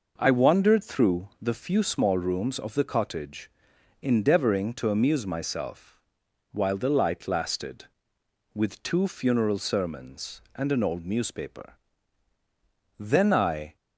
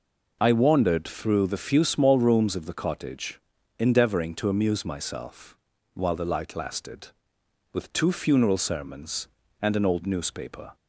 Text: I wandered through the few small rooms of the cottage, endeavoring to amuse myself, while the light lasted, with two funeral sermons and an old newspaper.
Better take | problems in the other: second | goes on to say "Then I"; noticeable; from 12.9 s on; 0.78 s long

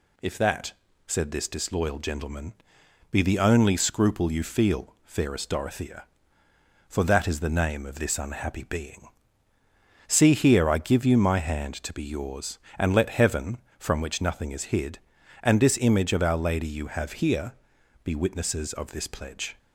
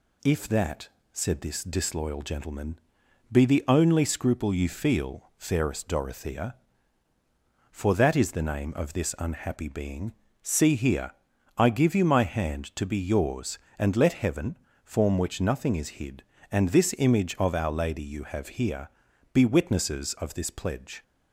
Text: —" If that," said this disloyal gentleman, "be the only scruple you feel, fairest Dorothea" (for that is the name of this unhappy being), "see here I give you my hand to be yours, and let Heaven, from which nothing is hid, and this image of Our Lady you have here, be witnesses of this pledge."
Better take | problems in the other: first | pauses between "here" and "I"; at 11.1 s; 0.44 s long // says "form" for "from"; at 14.8 s

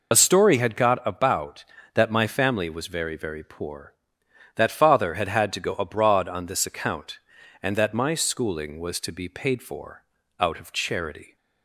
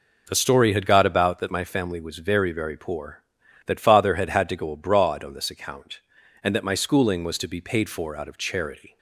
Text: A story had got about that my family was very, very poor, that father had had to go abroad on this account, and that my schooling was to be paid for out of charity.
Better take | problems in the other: second | loses the start of "A"; at 0.1 s; 40 ms // pauses between "for" and "out"; slight; at 10.0 s; 0.34 s long

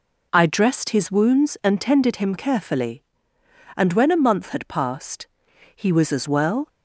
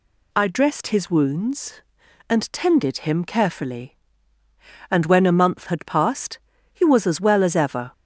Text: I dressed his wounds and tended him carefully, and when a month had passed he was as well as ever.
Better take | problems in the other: second | pauses between "passed" and "he"; noticeable; at 5.2 s; 0.50 s long; slight in the second // stops before "as ever"; at 6.6 s

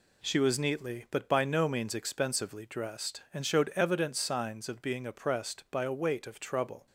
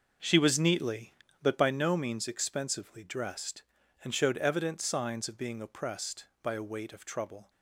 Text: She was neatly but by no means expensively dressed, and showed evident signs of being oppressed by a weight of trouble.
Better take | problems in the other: first | starts louder than the rest; until 1.8 s; 6 dB

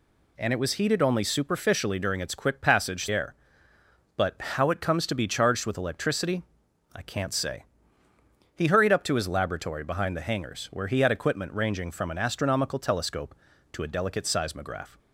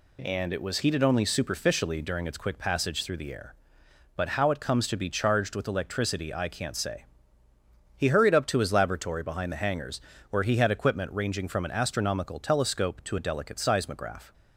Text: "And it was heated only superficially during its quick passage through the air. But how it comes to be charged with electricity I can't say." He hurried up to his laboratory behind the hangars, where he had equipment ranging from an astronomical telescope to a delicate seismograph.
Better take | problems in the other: second | skips "through the"; at 3.0 s // pauses between "electricity" and "I"; noticeable; at 6.4 s; 0.52 s long

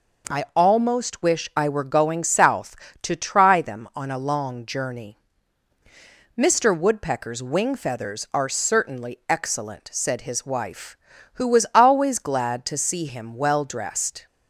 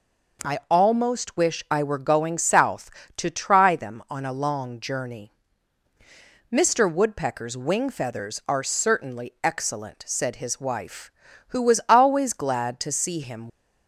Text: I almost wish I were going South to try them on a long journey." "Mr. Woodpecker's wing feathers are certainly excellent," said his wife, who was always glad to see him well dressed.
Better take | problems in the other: first | stops before "well dressed"; at 13.4 s

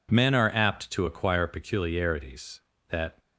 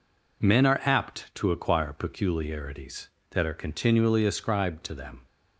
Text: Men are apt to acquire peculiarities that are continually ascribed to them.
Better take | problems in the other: second | stops before "are continually ascribed to them"; at 3.1 s

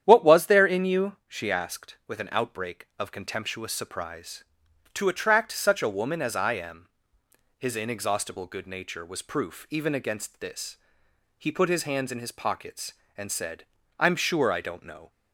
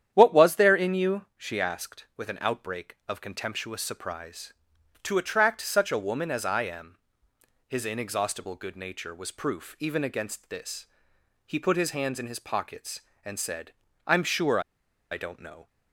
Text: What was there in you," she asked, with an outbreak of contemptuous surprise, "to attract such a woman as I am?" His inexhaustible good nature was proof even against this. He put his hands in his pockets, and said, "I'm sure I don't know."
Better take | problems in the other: first | starts louder than the rest; strong; until 1.1 s; 10 dB; strong in the first // pauses between "sure" and "I"; noticeable; at 14.5 s; 0.51 s long

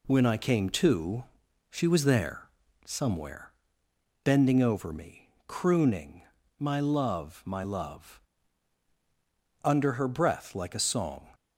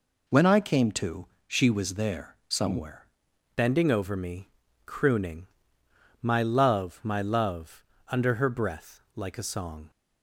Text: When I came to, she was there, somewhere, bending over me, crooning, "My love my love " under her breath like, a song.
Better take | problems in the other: first | changes voice at "bending"; from 3.5 s on; 6.4 s long

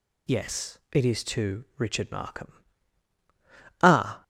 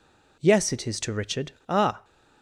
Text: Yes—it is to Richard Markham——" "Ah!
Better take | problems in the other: first | skips "Markham"; at 1.5 s

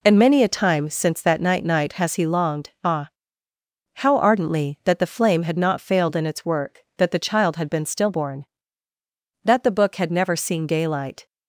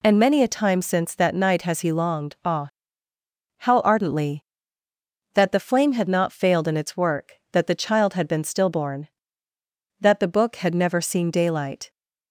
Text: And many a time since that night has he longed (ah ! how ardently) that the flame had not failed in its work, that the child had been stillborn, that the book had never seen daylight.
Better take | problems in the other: second | says "night" twice; at 1.6 s

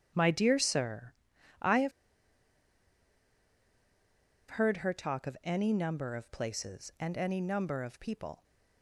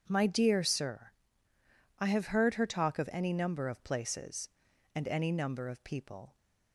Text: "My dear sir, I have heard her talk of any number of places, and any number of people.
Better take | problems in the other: second | starts louder than the rest; strong; until 1.1 s; 8.5 dB // pauses between "have" and "heard"; strong; at 1.9 s; 2.5 s long

